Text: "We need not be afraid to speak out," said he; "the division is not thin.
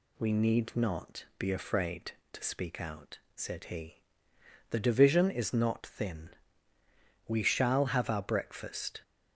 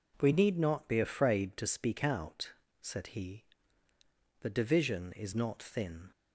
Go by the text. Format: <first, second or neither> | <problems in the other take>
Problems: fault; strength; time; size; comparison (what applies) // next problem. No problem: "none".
second | goes on to say "We shall have our breakfast"; strong; from 7.2 s on; 1.7 s long